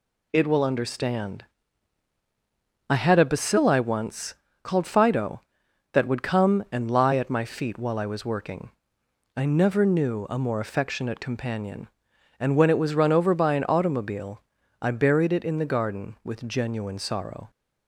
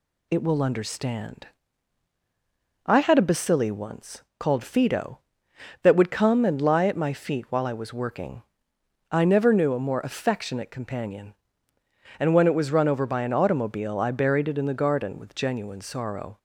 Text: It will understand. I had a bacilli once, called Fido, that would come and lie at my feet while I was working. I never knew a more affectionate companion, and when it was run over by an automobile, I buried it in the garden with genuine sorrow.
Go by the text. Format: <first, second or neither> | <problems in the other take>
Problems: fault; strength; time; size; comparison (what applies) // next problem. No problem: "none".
neither | none